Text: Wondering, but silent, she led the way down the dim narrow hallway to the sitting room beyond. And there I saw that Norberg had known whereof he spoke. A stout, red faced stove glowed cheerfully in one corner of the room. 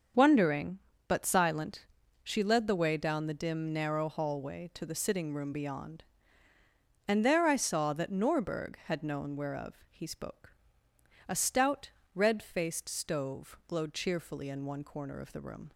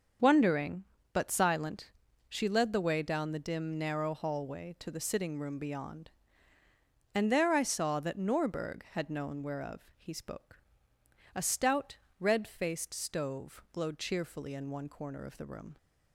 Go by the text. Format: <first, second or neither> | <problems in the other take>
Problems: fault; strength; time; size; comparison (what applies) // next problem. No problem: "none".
neither | starts louder than the rest; the same in both // pauses between "whereof" and "he"; slight; the same in both